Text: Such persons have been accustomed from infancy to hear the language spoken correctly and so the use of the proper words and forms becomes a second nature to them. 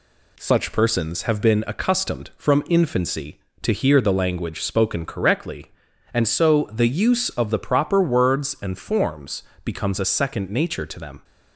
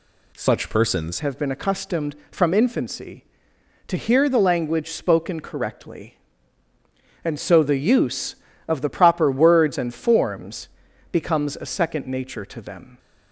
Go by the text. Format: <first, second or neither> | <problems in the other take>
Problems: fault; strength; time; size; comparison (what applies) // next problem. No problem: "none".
first | changes voice at "have"; from 1.1 s on; 11.8 s long // pauses between "forms" and "becomes"; at 10.6 s; 0.42 s long; slight in the first